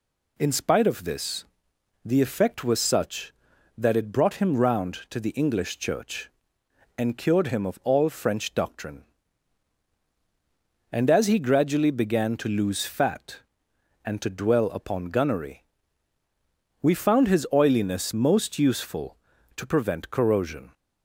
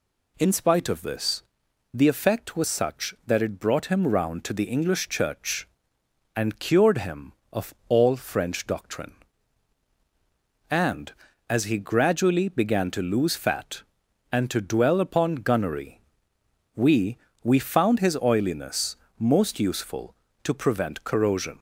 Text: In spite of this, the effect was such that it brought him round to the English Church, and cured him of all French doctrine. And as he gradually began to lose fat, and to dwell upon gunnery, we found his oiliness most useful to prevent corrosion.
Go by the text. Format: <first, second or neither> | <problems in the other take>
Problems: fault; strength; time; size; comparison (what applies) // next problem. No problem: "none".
first | says "we" twice; at 17.4 s // pauses between "oiliness" and "most"; slight; at 18.9 s; 0.20 s long